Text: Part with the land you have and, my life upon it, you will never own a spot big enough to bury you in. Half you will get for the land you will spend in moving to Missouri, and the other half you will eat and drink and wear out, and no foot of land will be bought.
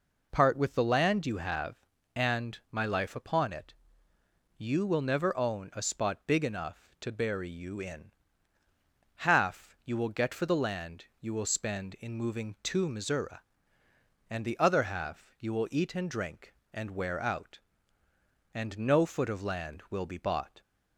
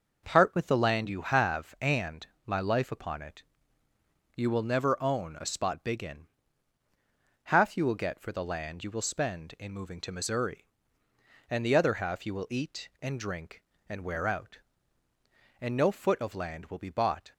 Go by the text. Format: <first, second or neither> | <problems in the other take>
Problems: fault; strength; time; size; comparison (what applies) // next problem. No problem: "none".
first | skips "enough to bury you"; at 6.0 s